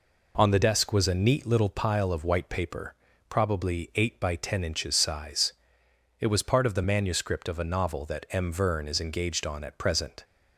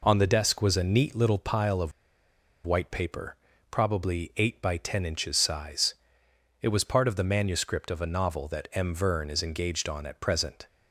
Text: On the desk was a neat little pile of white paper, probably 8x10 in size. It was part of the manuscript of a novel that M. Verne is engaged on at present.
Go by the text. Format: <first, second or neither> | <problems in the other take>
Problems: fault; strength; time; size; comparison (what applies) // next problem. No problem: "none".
first | pauses between "of" and "white"; noticeable; at 1.9 s; 0.74 s long